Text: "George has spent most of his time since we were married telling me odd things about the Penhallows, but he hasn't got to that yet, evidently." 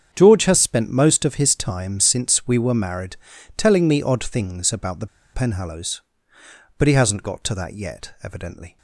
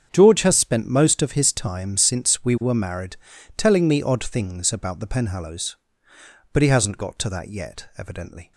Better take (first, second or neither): second